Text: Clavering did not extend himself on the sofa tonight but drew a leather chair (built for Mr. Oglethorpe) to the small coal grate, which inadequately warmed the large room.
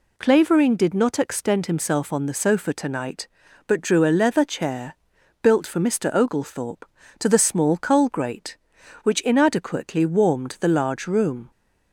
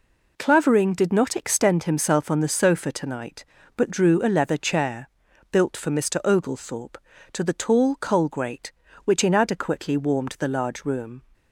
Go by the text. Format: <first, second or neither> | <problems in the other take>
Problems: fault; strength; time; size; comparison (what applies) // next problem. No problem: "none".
first | says "tall" for "small"; at 7.5 s